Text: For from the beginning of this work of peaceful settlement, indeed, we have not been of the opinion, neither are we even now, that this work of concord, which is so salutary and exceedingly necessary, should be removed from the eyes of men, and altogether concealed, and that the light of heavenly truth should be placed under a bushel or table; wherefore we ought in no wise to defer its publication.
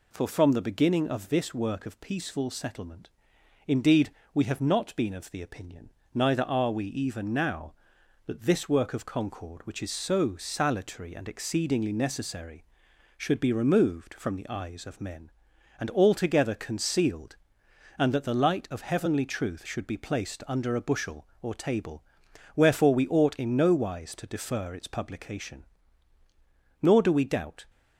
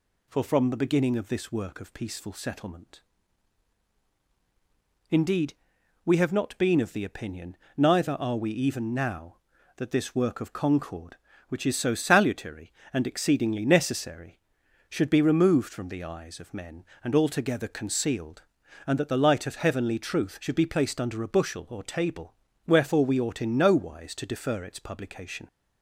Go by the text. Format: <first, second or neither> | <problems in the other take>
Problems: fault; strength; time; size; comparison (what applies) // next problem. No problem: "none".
second | goes on to say "Nor do we doubt"; noticeable; from 26.8 s on; 0.82 s long